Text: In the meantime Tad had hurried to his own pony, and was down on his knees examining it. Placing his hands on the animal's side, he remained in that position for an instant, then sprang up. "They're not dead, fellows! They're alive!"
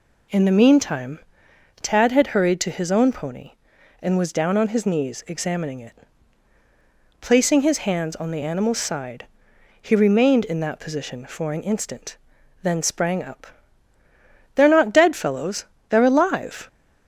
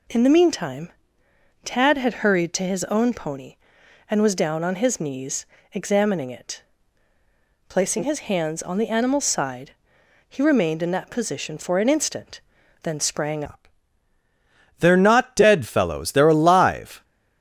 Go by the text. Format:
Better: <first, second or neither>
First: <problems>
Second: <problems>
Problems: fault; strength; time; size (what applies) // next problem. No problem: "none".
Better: first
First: pauses between "meantime" and "Tad"; noticeable; at 1.2 s; 0.60 s long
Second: pauses between "meantime" and "Tad"; noticeable; at 0.9 s; 0.74 s long // pauses between "knees" and "examining"; slight; at 5.4 s; 0.26 s long // changes voice at "up"; from 13.4 s on; 3.6 s long